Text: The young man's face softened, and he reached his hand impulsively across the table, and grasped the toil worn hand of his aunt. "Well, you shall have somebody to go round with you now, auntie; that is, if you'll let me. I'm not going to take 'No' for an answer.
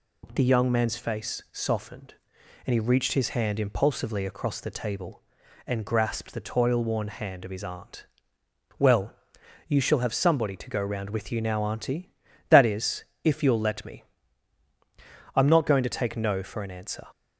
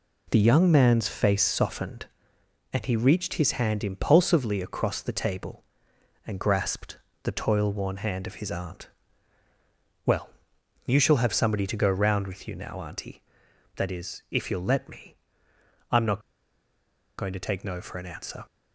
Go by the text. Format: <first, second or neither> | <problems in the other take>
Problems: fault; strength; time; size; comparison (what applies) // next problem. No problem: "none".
first | pauses between "grasped" and "the"; slight; at 6.9 s; 0.24 s long // pauses between "not" and "going"; noticeable; at 16.2 s; 0.97 s long